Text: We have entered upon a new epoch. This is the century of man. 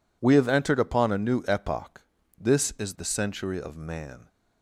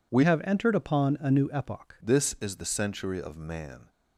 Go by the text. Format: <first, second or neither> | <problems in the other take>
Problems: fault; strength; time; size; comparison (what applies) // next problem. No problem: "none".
first | changes voice from "have" to "epoch"; from 0.2 to 1.9 s; 1.7 s long